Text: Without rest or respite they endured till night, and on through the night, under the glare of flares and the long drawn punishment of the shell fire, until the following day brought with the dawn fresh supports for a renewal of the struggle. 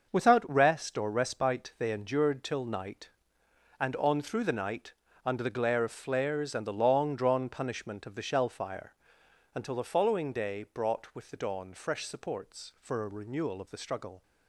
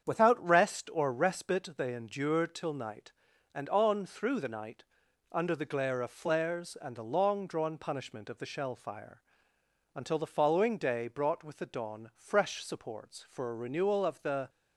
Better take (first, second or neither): first